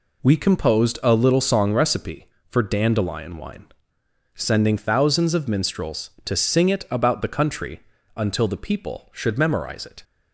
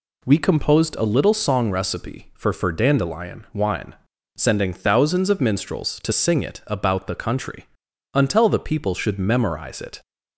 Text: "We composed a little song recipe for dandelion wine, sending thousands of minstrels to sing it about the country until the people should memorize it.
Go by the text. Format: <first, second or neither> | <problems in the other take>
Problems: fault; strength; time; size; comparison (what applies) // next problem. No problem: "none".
first | says "for" twice; at 2.5 s // pauses between "country" and "until"; noticeable; at 7.6 s; 0.46 s long; slight in the first